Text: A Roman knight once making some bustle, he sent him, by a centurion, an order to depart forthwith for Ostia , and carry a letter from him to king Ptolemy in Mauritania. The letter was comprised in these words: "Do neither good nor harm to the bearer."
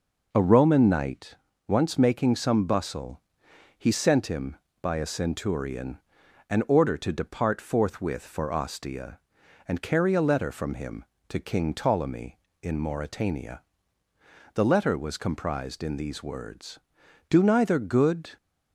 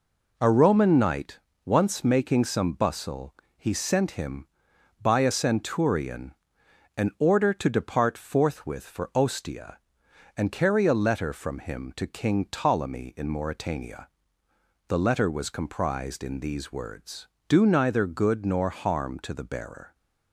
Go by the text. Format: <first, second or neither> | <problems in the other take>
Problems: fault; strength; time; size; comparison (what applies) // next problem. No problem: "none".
second | pauses between "knight" and "once"; slight; at 1.3 s; 0.32 s long; slight in the second // stops before "nor harm to the bearer"; at 18.3 s